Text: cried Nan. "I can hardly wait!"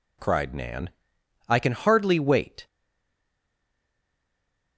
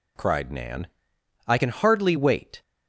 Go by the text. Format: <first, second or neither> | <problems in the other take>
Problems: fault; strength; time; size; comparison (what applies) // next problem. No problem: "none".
second | stays silent after the last word; from 2.6 s on; 2.1 s long